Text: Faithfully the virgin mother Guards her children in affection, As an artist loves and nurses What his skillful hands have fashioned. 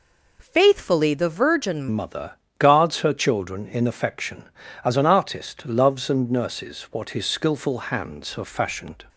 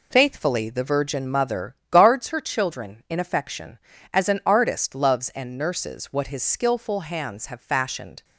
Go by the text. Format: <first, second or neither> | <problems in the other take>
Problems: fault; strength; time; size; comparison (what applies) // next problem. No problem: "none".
second | changes voice at "mother"; from 1.9 s on; 7.1 s long // pauses between "mother" and "Guards"; slight; at 2.3 s; 0.26 s long; slight in the second